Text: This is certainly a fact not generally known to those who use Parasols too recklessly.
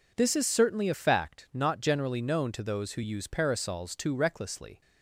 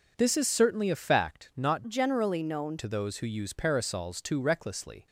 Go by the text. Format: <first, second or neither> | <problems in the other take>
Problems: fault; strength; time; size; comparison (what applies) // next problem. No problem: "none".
first | changes voice from "generally" to "known"; from 1.8 to 2.7 s; 0.9 s long